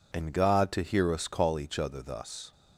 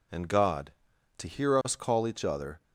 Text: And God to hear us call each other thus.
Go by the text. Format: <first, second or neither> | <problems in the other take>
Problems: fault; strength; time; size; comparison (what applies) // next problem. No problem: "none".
first | stops before "thus"; at 2.6 s